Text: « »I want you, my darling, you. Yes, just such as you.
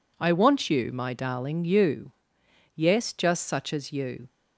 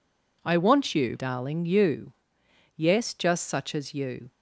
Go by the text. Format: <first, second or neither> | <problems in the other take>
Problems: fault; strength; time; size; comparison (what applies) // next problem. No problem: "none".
first | skips "my"; at 1.1 s